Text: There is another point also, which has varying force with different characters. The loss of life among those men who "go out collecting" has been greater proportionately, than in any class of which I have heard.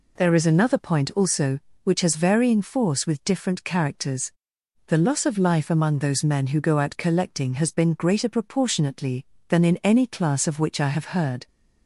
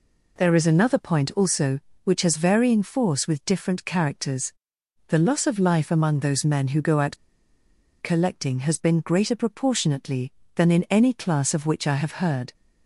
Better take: first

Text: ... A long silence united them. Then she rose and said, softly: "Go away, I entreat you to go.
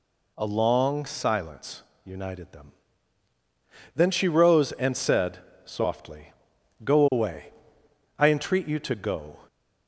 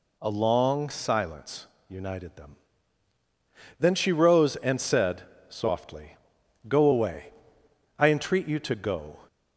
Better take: neither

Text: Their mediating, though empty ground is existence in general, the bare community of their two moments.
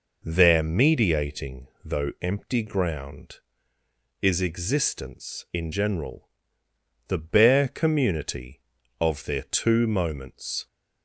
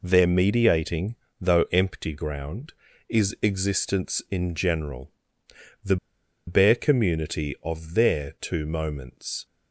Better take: first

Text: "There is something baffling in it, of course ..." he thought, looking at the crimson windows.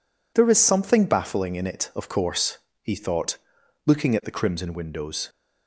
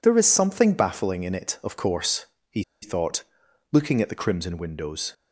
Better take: first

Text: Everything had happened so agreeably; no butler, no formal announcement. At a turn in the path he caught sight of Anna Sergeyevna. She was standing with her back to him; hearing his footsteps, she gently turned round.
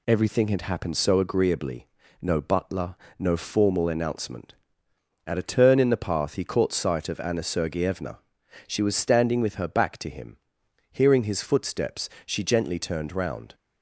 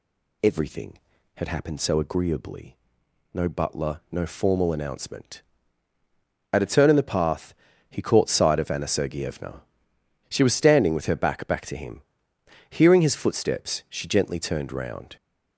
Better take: first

